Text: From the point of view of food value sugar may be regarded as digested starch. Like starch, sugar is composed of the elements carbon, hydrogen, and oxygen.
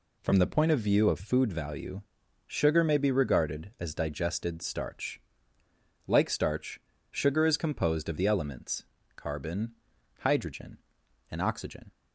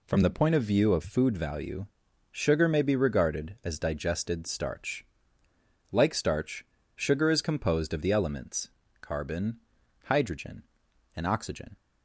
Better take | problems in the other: neither | pauses between "value" and "sugar"; the same in both // pauses between "elements" and "carbon"; slight; the same in both

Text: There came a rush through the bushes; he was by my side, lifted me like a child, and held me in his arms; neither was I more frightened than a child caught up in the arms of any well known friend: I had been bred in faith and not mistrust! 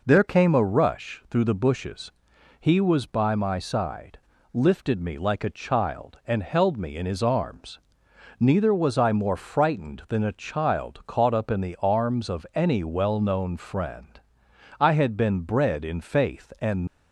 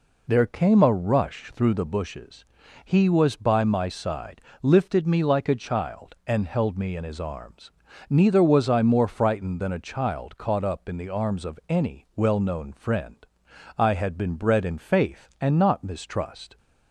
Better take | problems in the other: second | stops before "not mistrust"; at 16.8 s

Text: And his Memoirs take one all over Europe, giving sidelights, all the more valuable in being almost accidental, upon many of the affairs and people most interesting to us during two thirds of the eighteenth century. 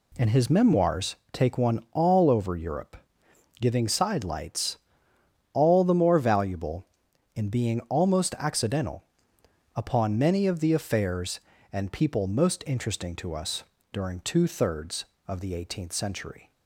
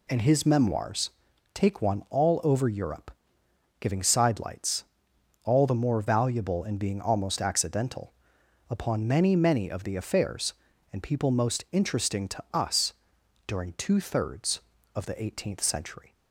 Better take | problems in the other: first | pauses between "Memoirs" and "take"; at 1.0 s; 0.44 s long; slight in the first // says "many" twice; at 9.3 s // pauses between "us" and "during"; noticeable; at 12.9 s; 0.54 s long; slight in the first

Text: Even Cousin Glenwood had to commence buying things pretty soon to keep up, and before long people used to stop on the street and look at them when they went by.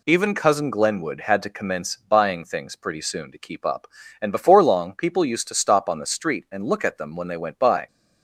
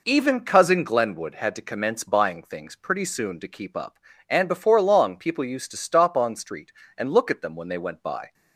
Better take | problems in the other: first | skips "the"; at 6.3 s

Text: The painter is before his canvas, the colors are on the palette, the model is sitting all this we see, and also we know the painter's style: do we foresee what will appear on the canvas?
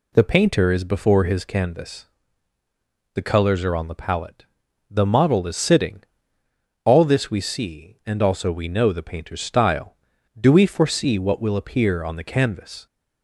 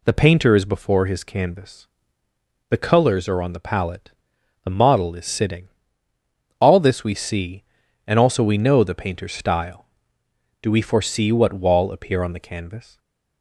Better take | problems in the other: first | pauses between "sitting" and "all"; noticeable; at 5.6 s; 0.90 s long; noticeable in the first // says "wall" for "will"; at 11.5 s // stays silent after the last word; slight; from 12.8 s on; 0.6 s long

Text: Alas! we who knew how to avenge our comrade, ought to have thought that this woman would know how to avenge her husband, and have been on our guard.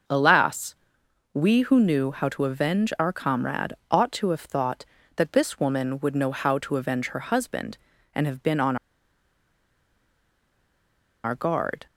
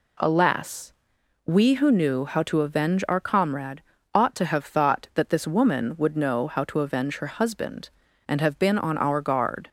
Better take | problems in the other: second | starts louder than the rest; noticeable; until 1.6 s; 6 dB // pauses between "on" and "our"; strong; at 8.7 s; 2.4 s long

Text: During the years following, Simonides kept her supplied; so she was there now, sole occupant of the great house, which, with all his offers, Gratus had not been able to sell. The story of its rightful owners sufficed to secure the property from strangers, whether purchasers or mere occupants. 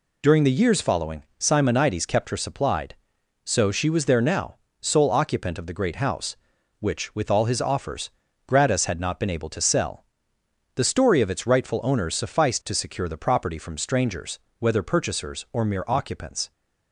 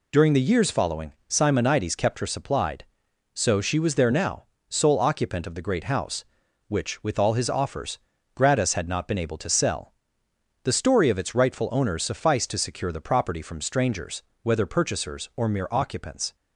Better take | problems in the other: neither | none

